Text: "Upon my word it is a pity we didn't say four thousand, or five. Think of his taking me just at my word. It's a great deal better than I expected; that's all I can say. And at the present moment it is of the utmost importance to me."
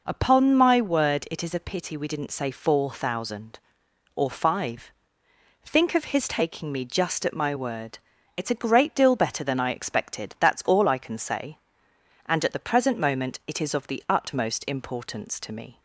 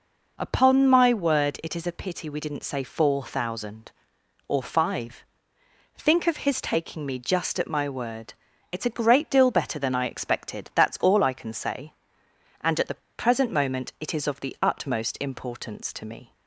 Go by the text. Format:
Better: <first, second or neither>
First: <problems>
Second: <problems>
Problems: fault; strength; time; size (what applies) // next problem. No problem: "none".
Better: first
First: none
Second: pauses between "the" and "present"; slight; at 13.0 s; 0.19 s long